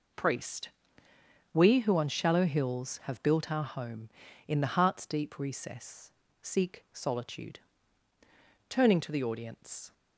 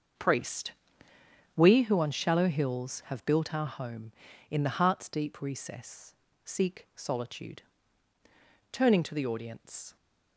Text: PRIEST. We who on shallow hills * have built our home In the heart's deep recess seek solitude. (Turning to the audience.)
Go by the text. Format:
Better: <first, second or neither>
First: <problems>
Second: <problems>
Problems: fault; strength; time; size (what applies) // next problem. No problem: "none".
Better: first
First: pauses between "recess" and "seek"; slight; at 6.1 s; 0.32 s long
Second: starts louder than the rest; until 1.9 s; 6.5 dB // pauses between "recess" and "seek"; slight; at 6.1 s; 0.32 s long